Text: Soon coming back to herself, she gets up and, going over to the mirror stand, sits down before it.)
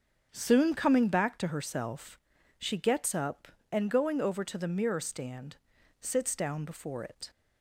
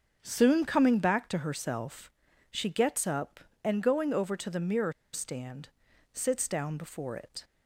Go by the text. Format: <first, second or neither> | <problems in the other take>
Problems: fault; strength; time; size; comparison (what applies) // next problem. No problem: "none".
first | starts louder than the rest; until 1.2 s; 7 dB; strong in the first // pauses between "mirror" and "stand"; slight; at 4.9 s; 0.21 s long